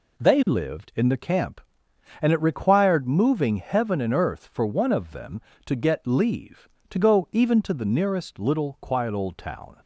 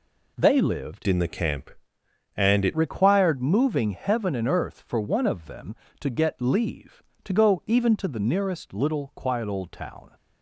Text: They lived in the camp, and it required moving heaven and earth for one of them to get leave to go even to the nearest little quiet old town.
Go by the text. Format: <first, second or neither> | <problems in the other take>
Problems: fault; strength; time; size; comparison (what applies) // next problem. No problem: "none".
first | changes voice from "in" to "it"; from 1.0 to 2.7 s; 1.7 s long